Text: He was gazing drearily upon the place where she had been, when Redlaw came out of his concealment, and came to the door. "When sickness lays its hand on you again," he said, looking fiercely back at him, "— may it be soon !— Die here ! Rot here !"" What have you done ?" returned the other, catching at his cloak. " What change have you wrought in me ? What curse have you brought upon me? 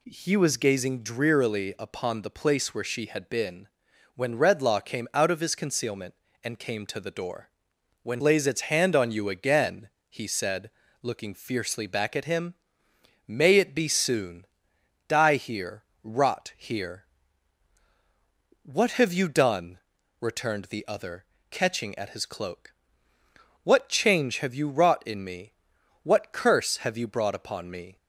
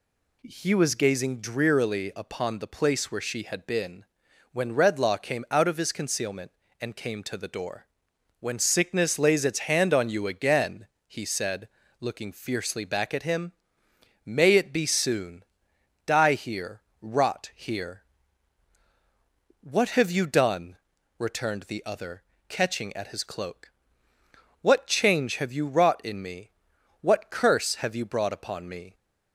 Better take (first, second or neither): second